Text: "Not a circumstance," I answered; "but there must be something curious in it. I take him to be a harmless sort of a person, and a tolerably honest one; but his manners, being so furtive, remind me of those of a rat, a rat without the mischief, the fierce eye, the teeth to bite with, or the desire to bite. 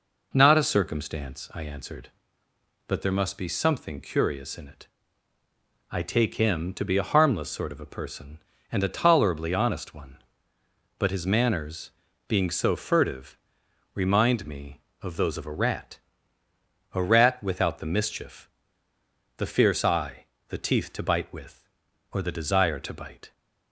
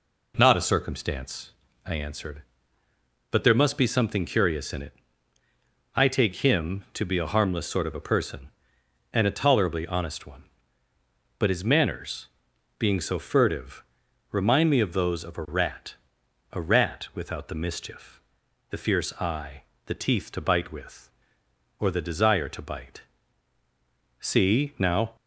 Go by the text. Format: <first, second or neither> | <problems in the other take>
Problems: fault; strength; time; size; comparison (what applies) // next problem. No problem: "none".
first | goes on to say "See now"; noticeable; from 24.1 s on; 0.96 s long